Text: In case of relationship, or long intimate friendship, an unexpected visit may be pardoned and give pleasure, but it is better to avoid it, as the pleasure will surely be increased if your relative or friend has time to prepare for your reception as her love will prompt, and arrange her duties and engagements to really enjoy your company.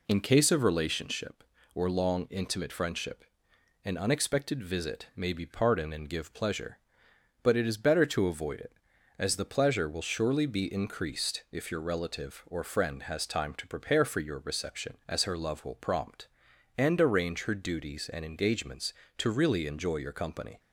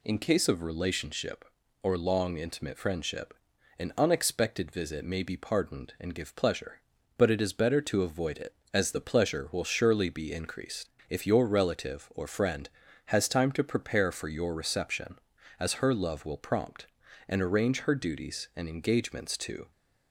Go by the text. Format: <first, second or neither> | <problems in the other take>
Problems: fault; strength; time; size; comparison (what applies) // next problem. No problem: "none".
first | pauses between "increased" and "if"; slight; at 10.8 s; 0.22 s long // stops before "really enjoy your company"; at 19.7 s